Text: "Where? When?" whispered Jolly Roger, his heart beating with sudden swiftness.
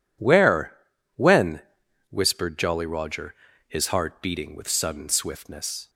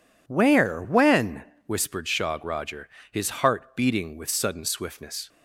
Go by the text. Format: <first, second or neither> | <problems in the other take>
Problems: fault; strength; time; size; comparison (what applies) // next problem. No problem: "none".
first | says "Shog" for "Jolly"; at 2.0 s